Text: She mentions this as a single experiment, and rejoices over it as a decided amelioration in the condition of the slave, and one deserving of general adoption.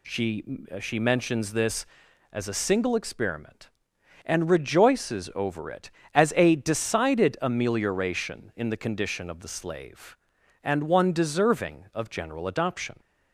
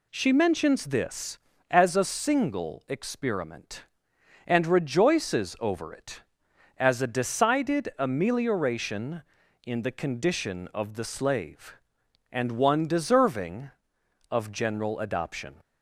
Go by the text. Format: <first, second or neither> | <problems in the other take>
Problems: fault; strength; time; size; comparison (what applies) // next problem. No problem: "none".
second | says "She" twice; at 0.7 s